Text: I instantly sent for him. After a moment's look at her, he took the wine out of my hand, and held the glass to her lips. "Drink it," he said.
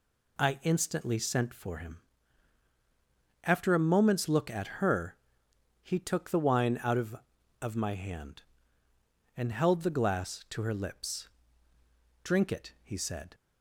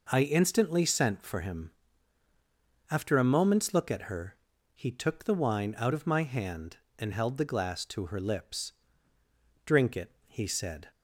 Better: second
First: says "of" twice; at 7.6 s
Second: none

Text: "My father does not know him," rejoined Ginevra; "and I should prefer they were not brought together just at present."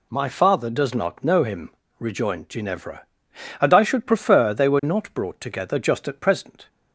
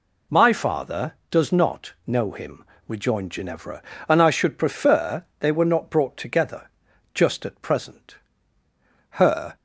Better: first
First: none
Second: pauses between "together" and "just"; at 6.6 s; 0.44 s long // goes on to say "Her"; slight; from 9.2 s on; 0.34 s long

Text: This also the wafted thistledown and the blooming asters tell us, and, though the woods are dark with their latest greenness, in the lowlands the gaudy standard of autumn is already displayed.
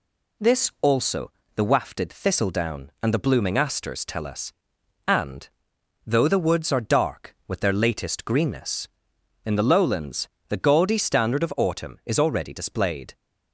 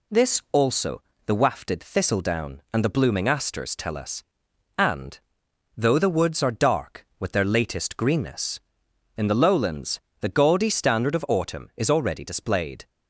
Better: neither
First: pauses between "also" and "the"; slight; at 1.3 s; 0.24 s long // pauses between "lowlands" and "the"; slight; at 10.2 s; 0.20 s long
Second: pauses between "also" and "the"; slight; at 1.0 s; 0.24 s long // pauses between "lowlands" and "the"; slight; at 10.0 s; 0.20 s long

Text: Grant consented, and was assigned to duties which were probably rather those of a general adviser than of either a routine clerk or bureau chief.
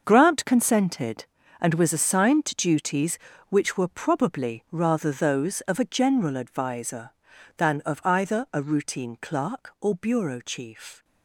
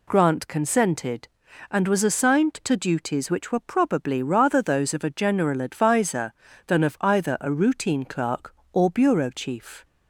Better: second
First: gets quieter; strong; throughout; 12 dB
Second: none

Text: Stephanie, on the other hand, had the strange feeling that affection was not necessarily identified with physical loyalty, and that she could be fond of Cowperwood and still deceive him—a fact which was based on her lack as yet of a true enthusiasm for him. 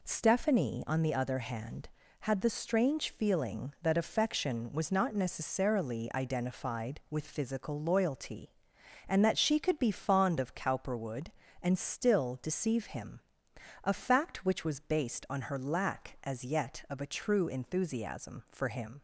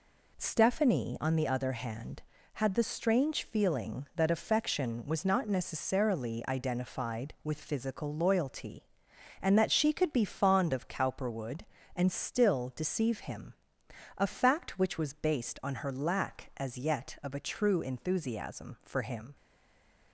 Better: first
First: none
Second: stays silent after the last word; slight; from 19.3 s on; 0.8 s long

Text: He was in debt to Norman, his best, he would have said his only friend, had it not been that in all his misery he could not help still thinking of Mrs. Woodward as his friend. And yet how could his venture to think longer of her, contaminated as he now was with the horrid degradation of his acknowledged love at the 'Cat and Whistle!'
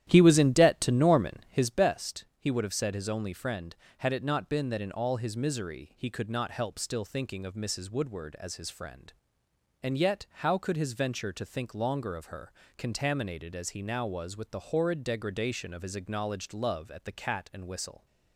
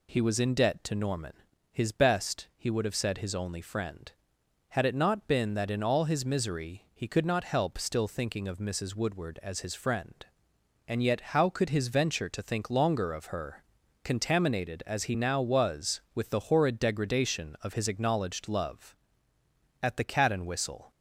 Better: second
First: starts louder than the rest; strong; until 1.7 s; 11.5 dB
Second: none

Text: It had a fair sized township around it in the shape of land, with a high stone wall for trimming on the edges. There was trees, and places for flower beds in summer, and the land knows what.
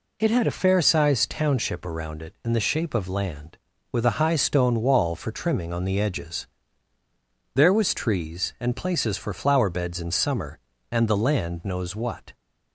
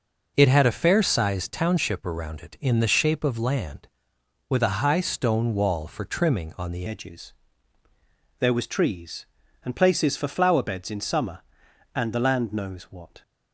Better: first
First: none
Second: changes voice at "edges"; from 6.8 s on; 6.4 s long

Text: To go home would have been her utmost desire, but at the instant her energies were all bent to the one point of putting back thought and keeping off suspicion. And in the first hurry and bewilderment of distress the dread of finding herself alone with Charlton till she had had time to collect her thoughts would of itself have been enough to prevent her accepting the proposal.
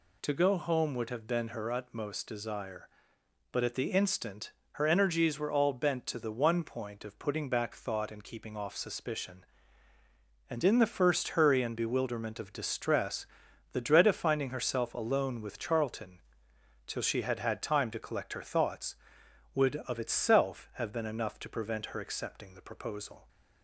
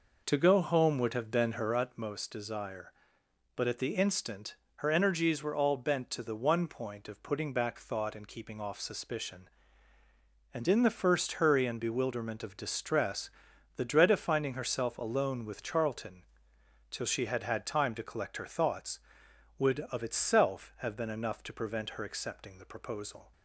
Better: first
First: pauses between "instant" and "her"; slight; at 4.5 s; 0.20 s long // pauses between "distress" and "the"; noticeable; at 13.2 s; 0.48 s long // pauses between "Charlton" and "till"; noticeable; at 16.1 s; 0.68 s long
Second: starts louder than the rest; noticeable; until 2.0 s; 5 dB // pauses between "instant" and "her"; slight; at 4.5 s; 0.20 s long // pauses between "distress" and "the"; noticeable; at 13.2 s; 0.48 s long // pauses between "Charlton" and "till"; noticeable; at 16.2 s; 0.68 s long

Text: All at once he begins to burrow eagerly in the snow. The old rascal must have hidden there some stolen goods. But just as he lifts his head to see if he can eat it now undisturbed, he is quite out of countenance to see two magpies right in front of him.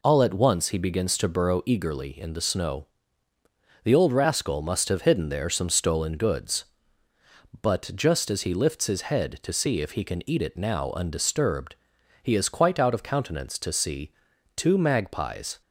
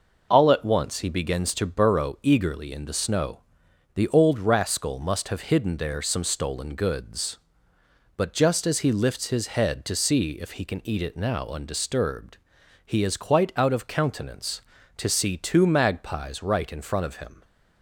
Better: second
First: pauses between "see" and "two"; noticeable; at 14.1 s; 0.46 s long // stops before "right in front of him"; at 15.6 s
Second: none

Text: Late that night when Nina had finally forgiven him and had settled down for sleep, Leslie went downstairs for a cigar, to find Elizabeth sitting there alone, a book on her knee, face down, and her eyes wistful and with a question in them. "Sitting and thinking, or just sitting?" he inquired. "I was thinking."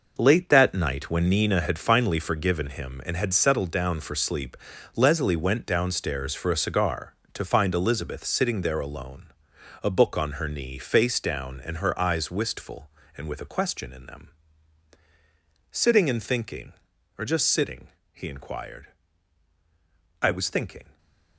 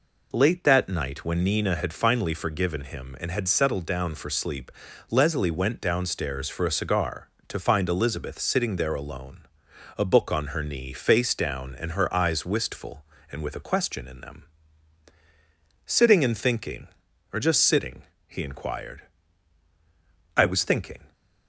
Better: second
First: gets quieter; strong; throughout; 10.5 dB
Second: none

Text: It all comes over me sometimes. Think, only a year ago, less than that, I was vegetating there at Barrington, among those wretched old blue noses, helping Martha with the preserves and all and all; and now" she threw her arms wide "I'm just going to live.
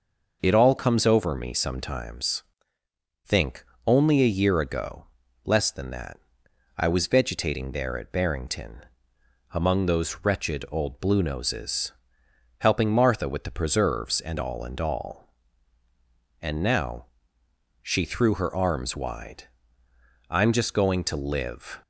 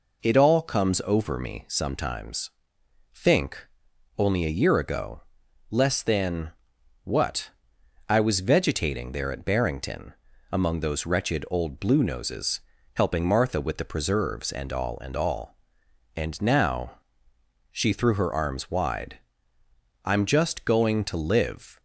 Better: first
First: pauses between "now" and "she"; noticeable; at 17.0 s; 0.78 s long // pauses between "wide" and "I'm"; noticeable; at 19.4 s; 0.86 s long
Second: says "what" for "that"; at 7.0 s // pauses between "now" and "she"; noticeable; at 16.9 s; 0.72 s long // pauses between "wide" and "I'm"; noticeable; at 19.1 s; 0.84 s long

